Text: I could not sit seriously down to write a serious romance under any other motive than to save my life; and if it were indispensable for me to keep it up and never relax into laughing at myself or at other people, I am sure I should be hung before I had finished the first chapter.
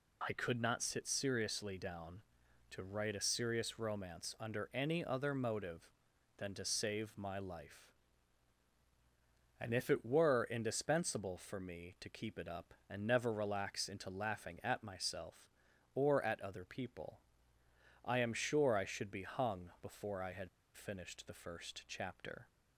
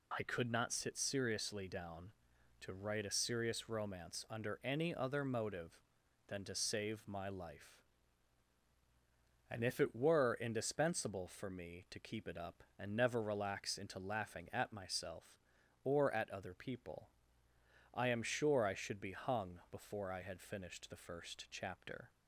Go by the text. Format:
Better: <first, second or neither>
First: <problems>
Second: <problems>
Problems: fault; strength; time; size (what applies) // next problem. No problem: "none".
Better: second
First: pauses between "had" and "finished"; slight; at 20.4 s; 0.27 s long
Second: none